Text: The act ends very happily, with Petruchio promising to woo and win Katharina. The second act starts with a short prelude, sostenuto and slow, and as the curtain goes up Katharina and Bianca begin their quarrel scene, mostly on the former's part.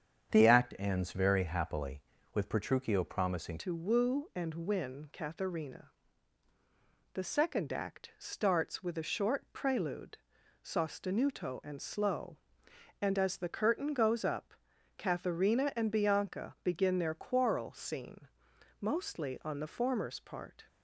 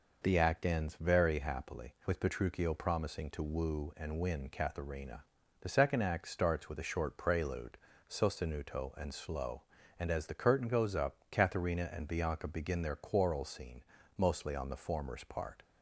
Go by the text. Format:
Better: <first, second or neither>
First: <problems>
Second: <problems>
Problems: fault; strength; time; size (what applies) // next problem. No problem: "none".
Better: second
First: starts louder than the rest; strong; until 1.3 s; 7.5 dB // changes voice at "to"; from 3.5 s on; 17.1 s long // pauses between "up" and "Katharina"; at 14.5 s; 0.42 s long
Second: pauses between "up" and "Katharina"; slight; at 11.1 s; 0.16 s long